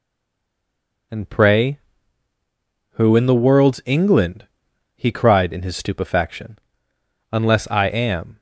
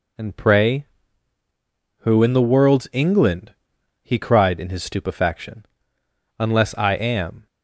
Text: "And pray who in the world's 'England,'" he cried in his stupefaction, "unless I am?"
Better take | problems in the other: second | stays silent before the first word; until 1.1 s; 1.1 s long

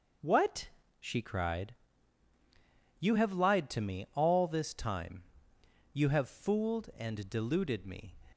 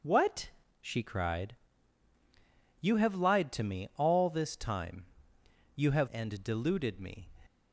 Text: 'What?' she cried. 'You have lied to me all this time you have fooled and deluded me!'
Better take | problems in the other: first | pauses between "time" and "you"; noticeable; at 5.0 s; 0.70 s long; noticeable in the first // skips "fooled"; at 6.0 s

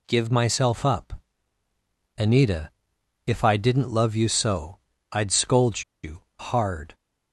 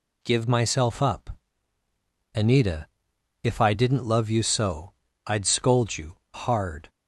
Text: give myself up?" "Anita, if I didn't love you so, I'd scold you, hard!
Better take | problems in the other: second | pauses between "scold" and "you"; slight; at 5.8 s; 0.21 s long

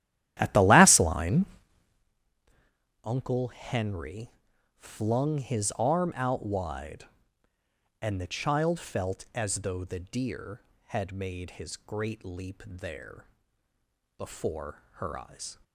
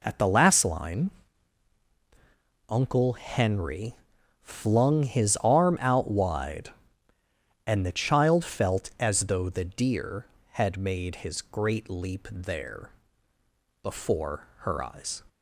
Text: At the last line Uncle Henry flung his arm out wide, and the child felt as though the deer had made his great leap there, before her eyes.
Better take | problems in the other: second | starts louder than the rest; strong; until 2.1 s; 12.5 dB // pauses between "line" and "Uncle"; strong; at 1.4 s; 1.5 s long; strong in the second // pauses between "Henry" and "flung"; noticeable; at 4.2 s; 0.46 s long; noticeable in the second

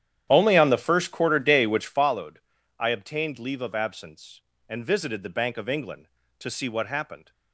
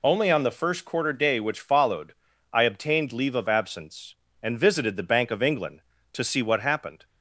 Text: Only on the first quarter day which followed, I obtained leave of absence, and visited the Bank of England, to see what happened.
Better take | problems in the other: second | starts louder than the rest; strong; until 2.2 s; 10 dB

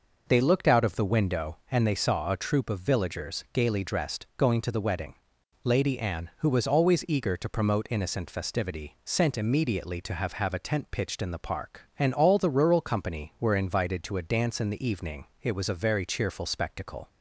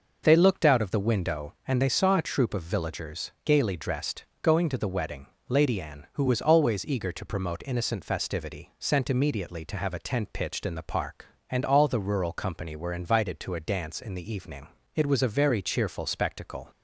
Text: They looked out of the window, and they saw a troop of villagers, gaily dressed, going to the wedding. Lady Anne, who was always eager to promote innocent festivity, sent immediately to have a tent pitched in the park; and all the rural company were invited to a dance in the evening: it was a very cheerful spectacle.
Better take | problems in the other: second | says "have" twice; at 10.3 s

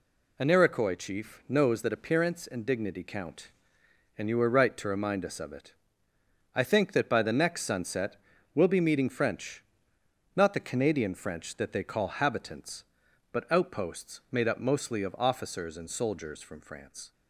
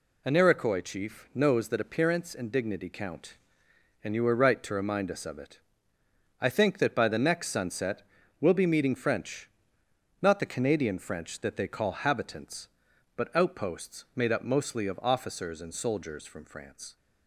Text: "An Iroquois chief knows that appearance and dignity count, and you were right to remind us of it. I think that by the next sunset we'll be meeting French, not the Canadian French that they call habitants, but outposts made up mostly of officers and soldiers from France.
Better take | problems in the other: neither | pauses between "sunset" and "we'll"; the same in both

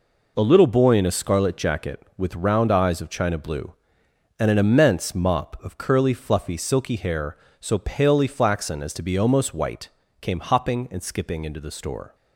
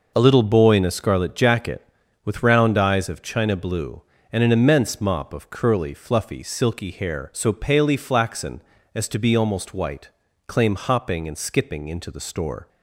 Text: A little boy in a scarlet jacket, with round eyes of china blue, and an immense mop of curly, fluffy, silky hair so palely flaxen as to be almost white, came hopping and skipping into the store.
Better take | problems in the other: first | says "claim" for "came"; at 10.4 s

